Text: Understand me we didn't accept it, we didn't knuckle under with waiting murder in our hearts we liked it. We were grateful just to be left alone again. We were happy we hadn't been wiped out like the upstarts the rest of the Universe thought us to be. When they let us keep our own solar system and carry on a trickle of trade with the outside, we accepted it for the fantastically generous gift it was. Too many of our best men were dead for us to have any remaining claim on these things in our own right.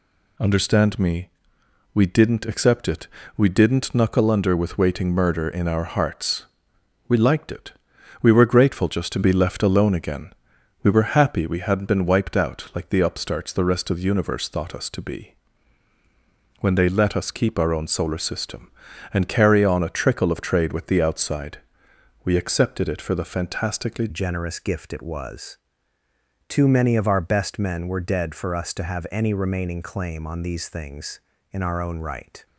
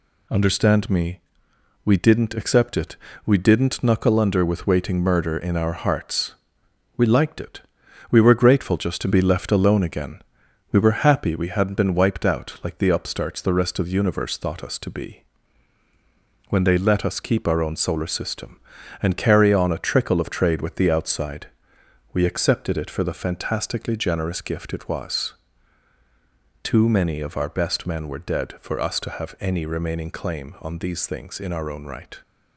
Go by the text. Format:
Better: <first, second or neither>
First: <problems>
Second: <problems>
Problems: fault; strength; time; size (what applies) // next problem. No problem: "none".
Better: second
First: pauses between "me" and "we"; noticeable; at 1.2 s; 0.64 s long // pauses between "hearts" and "we"; noticeable; at 6.4 s; 0.60 s long // changes voice at "generous"; from 24.0 s on; 8.4 s long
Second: pauses between "me" and "we"; noticeable; at 1.1 s; 0.64 s long // pauses between "hearts" and "we"; noticeable; at 6.3 s; 0.60 s long